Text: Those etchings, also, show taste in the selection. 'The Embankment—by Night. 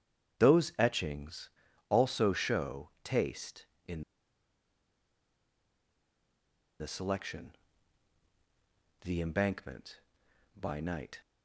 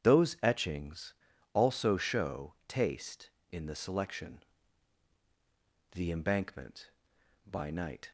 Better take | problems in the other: second | starts louder than the rest; strong; until 1.4 s; 8.5 dB; strong in the second // pauses between "in" and "the"; strong; at 4.0 s; 2.7 s long

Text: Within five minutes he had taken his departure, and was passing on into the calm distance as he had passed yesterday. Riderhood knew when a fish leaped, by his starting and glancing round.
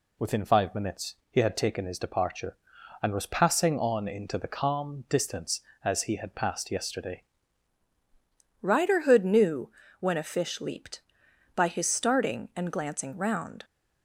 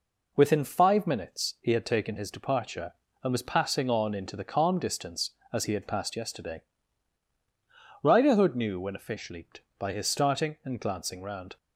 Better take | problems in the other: second | pauses between "minutes" and "he"; slight; at 1.1 s; 0.16 s long // changes voice at "Riderhood"; from 8.6 s on; 5.0 s long // pauses between "knew" and "when"; slight; at 9.7 s; 0.30 s long

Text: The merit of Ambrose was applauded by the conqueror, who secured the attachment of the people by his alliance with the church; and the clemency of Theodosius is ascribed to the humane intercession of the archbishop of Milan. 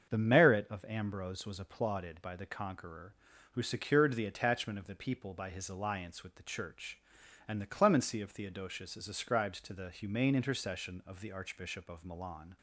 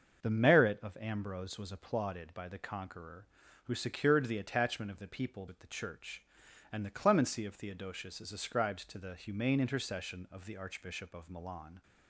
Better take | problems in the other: first | starts louder than the rest; until 1.2 s; 6.5 dB; also in the first // skips "by his alliance"; at 5.4 s

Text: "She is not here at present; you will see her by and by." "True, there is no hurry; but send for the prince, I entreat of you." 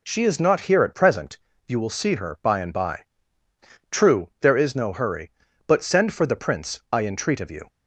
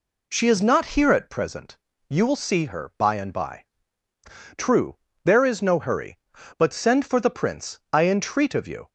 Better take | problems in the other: neither | none

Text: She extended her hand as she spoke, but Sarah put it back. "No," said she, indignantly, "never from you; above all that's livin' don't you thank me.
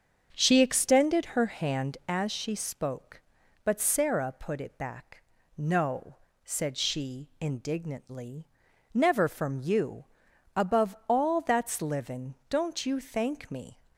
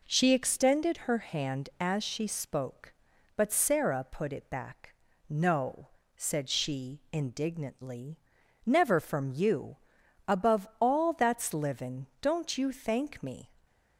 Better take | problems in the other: second | starts louder than the rest; until 2.1 s; 6.5 dB

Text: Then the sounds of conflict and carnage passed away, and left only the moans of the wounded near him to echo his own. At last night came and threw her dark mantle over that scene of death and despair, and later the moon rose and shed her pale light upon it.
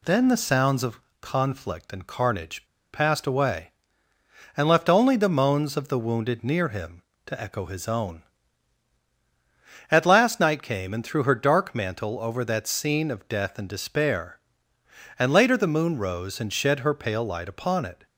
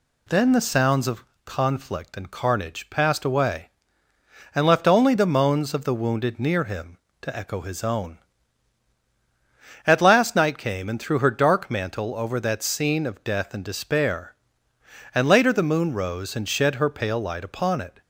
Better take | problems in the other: second | pauses between "of" and "conflict"; slight; at 0.9 s; 0.22 s long; slight in the second // pauses between "carnage" and "passed"; slight; at 2.6 s; 0.27 s long

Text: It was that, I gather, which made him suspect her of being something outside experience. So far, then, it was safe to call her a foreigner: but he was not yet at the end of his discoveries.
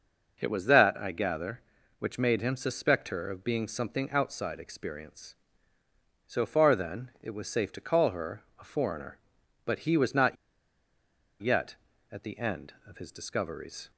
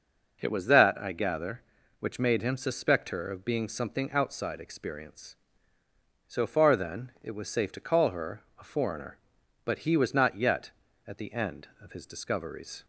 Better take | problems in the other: second | pauses between "her" and "a"; slight; at 8.4 s; 0.16 s long; slight in the second // pauses between "not" and "yet"; at 10.3 s; 1.0 s long

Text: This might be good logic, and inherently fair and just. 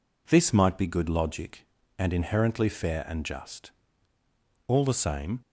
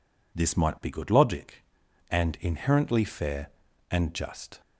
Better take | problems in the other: second | goes on to say "All the same"; noticeable; from 4.6 s on; 0.72 s long

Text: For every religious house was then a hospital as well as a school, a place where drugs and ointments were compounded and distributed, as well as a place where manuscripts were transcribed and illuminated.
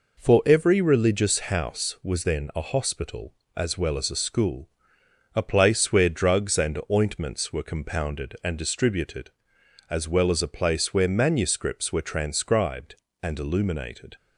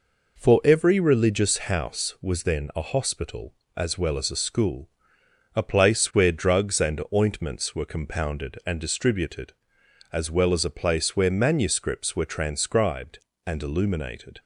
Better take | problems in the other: neither | none

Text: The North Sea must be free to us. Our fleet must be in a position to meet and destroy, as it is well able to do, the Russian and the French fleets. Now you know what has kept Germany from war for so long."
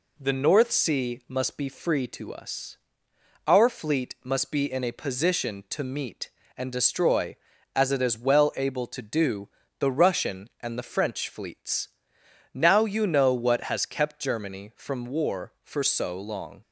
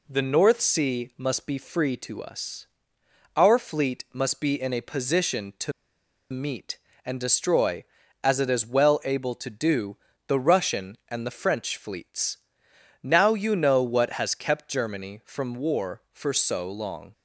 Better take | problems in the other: first | pauses between "to" and "meet"; noticeable; at 5.7 s; 0.60 s long

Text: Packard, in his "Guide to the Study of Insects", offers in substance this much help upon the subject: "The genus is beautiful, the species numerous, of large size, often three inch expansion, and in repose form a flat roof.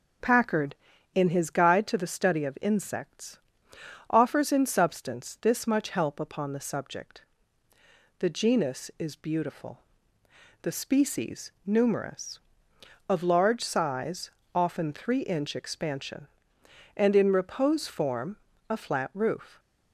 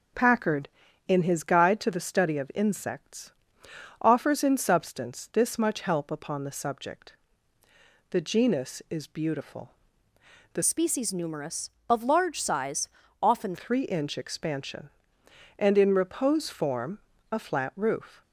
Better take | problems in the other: first | changes voice from "species" to "often"; from 10.6 to 13.5 s; 2.9 s long // pauses between "form" and "a"; slight; at 16.9 s; 0.32 s long; slight in the first

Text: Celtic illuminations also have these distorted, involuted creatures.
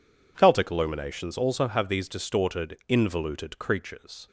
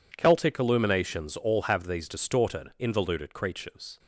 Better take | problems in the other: first | says "all" for "also"; at 1.3 s

